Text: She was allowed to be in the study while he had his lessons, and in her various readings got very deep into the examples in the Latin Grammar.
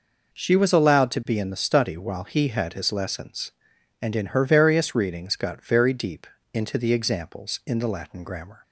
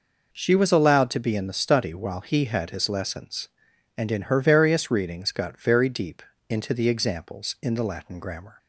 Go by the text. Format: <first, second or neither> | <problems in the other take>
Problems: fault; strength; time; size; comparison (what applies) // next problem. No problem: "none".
neither | pauses between "deep" and "into"; slight; the same in both